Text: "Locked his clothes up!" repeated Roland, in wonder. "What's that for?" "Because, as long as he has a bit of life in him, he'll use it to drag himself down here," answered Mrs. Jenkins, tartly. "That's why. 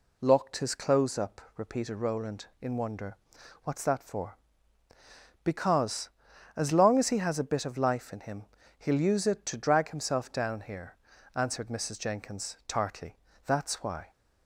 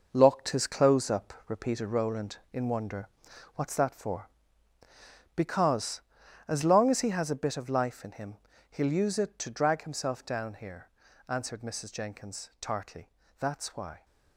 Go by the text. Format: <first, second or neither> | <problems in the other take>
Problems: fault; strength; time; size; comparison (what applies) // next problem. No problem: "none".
first | gets quieter; strong; throughout; 9 dB